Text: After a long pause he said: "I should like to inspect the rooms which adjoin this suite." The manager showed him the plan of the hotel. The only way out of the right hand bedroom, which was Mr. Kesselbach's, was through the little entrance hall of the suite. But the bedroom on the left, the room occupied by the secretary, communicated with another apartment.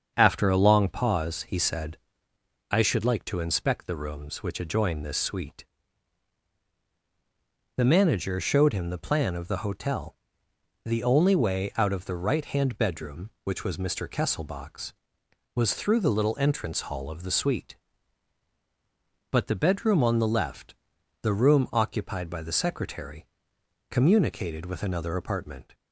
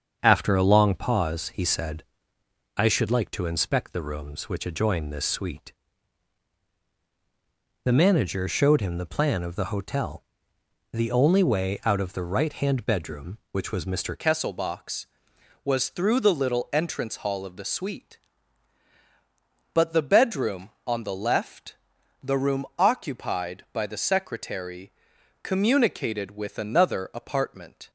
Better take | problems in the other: first | starts louder than the rest; strong; until 1.2 s; 7 dB; also in the first // changes voice at "Kesselbach's"; from 14.1 s on; 13.7 s long

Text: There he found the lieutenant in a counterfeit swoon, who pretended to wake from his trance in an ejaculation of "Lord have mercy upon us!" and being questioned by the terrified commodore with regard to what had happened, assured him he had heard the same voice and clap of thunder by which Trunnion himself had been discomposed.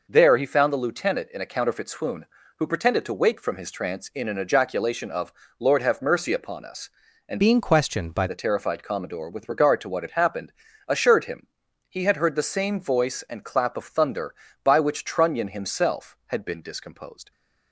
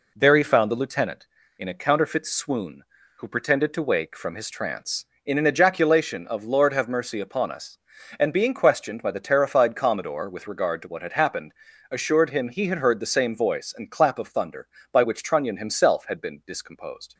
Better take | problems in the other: second | pauses between "of" and "Lord"; slight; at 5.3 s; 0.28 s long // changes voice from "being" to "by"; from 7.4 to 8.2 s; 0.8 s long // pauses between "him" and "he"; at 11.4 s; 0.40 s long

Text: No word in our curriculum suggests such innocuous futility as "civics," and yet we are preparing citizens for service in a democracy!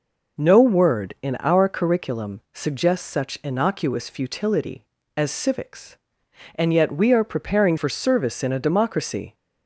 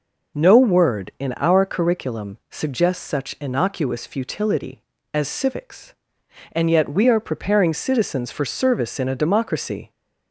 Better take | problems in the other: second | skips "citizens"; at 7.7 s

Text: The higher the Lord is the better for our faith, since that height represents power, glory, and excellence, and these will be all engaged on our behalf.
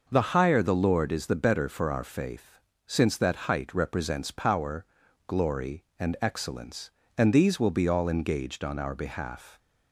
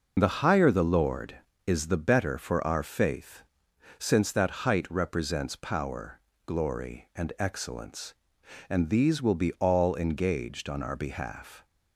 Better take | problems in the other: first | loses the start of "The"; at 0.1 s; 30 ms

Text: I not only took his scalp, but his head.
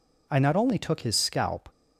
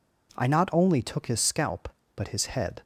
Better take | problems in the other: second | stops before "but his head"; at 1.7 s

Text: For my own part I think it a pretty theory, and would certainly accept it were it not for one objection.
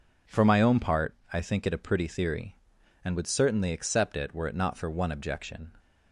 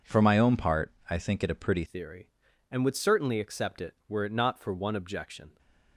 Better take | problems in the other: first | pauses between "part" and "I"; slight; at 0.9 s; 0.18 s long; slight in the first // changes voice at "theory"; from 1.8 s on; 3.7 s long

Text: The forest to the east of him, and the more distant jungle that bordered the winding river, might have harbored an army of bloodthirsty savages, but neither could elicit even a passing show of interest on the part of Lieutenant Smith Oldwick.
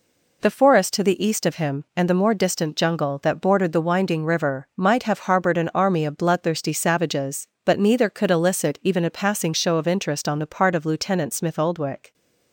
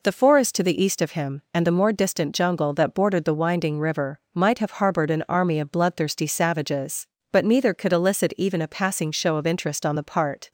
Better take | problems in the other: first | stops before "of Lieutenant Smith Oldwick"; at 10.4 s

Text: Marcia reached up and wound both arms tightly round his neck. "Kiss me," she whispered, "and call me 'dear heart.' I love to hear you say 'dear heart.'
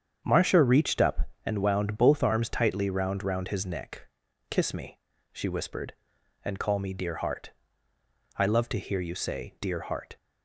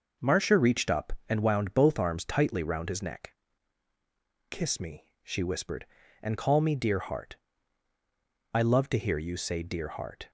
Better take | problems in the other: second | starts louder than the rest; strong; until 1.2 s; 7.5 dB // says "round" twice; at 3.2 s

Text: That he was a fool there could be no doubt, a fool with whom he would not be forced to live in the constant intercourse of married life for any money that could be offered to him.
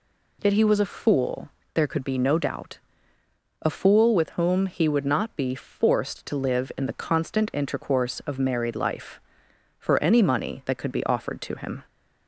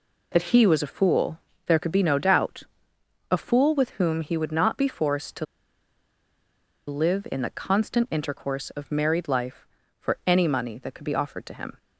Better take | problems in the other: first | pauses between "fool" and "there"; slight; at 1.3 s; 0.30 s long; slight in the first // pauses between "to" and "live"; strong; at 5.4 s; 1.4 s long

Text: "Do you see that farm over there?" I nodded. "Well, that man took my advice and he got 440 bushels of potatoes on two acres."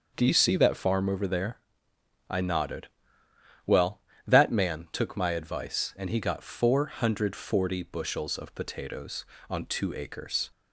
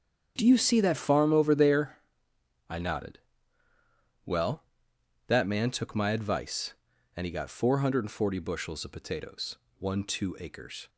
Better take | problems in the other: first | starts louder than the rest; strong; until 1.3 s; 7.5 dB; also in the first // says "one" for "on"; at 9.7 s

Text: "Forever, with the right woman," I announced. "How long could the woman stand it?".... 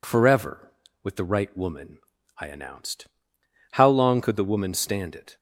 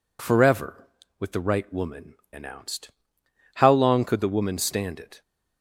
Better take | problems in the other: first | skips "I"; at 2.2 s

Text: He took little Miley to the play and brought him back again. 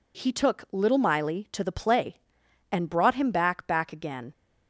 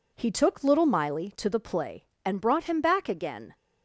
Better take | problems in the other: second | says "back" twice; at 3.6 s

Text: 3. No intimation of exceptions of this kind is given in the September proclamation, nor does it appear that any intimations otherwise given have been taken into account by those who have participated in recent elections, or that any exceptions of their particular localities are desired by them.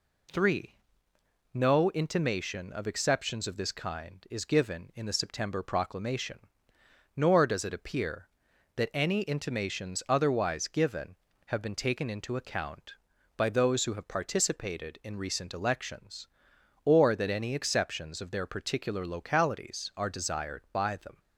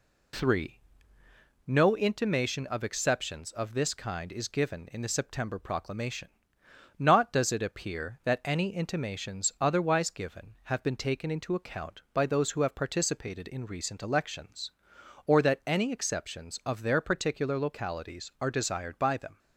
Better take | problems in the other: first | says "not" for "nor"; at 6.9 s

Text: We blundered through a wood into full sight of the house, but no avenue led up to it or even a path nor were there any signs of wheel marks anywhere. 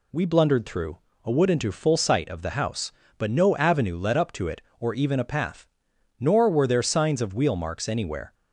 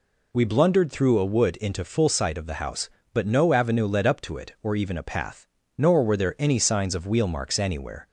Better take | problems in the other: second | pauses between "through" and "a"; slight; at 0.9 s; 0.26 s long // pauses between "path" and "nor"; noticeable; at 5.6 s; 0.56 s long; slight in the second // skips "any"; at 6.8 s

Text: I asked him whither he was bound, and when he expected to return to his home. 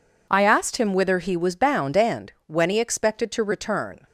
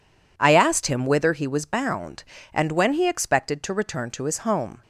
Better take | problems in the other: second | stops before "to his home"; at 4.0 s

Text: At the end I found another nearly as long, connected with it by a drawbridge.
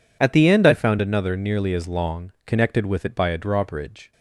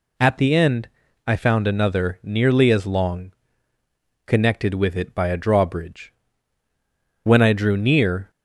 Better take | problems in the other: first | pauses between "end" and "I"; at 0.8 s; 0.38 s long // goes on to say "When I drew near"; noticeable; from 7.2 s on; 1.0 s long

